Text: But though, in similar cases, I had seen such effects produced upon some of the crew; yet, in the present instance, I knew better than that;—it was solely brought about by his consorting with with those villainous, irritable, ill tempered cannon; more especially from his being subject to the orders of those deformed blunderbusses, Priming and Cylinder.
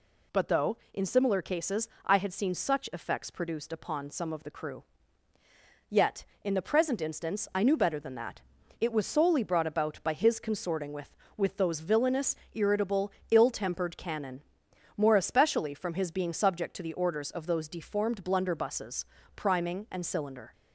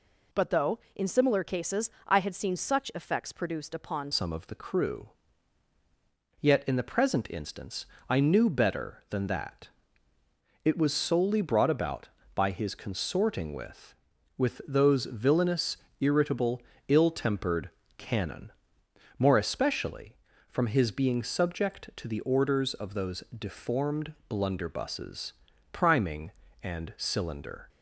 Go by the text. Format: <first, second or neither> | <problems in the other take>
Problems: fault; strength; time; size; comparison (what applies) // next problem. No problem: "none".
first | changes voice at "some"; from 4.1 s on; 23.5 s long // pauses between "tempered" and "cannon"; slight; at 17.6 s; 0.30 s long